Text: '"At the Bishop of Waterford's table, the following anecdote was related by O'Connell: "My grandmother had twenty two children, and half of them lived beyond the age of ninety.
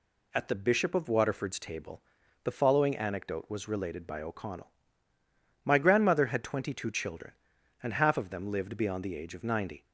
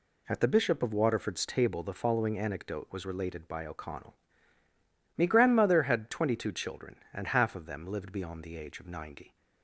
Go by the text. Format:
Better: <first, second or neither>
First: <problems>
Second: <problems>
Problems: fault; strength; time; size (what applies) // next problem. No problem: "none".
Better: first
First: none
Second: says "Me" for "My"; at 5.1 s